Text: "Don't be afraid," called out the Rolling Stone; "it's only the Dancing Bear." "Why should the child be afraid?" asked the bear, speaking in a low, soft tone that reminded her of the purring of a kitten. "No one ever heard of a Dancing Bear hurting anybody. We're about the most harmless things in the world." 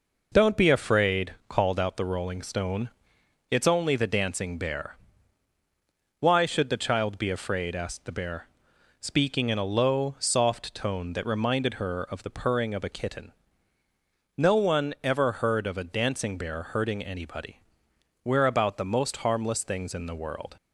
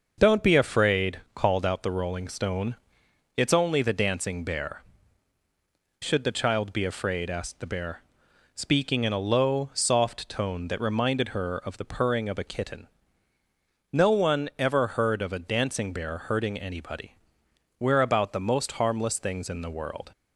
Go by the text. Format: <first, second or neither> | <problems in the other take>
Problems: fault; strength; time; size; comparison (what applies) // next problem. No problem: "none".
first | starts louder than the rest; noticeable; until 1.1 s; 6 dB // skips "Why"; at 5.4 s